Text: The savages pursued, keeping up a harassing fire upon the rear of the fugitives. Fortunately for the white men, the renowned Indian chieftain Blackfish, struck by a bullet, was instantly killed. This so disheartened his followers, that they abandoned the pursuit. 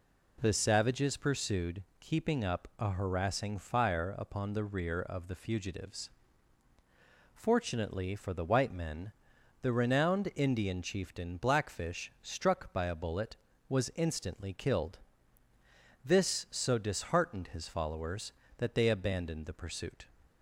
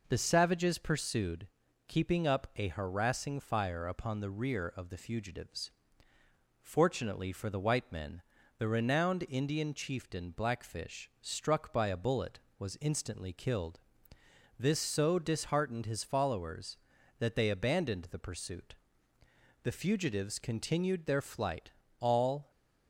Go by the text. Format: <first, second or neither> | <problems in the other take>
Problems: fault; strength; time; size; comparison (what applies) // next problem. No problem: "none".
first | goes on to say "The fugitives continued their flight all"; strong; from 19.6 s on; 2.8 s long